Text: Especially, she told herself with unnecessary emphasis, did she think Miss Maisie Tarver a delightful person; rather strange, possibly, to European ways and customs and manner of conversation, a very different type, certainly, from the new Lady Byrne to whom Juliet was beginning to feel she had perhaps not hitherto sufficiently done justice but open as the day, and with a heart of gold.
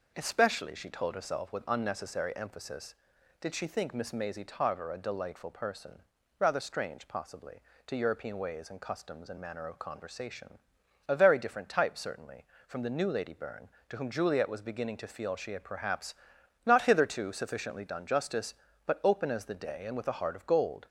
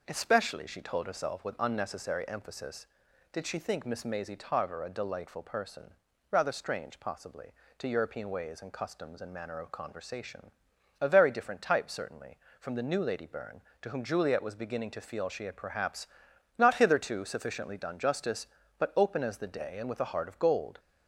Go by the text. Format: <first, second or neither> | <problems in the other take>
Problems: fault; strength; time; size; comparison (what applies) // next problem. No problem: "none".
neither | pauses between "perhaps" and "not"; noticeable; the same in both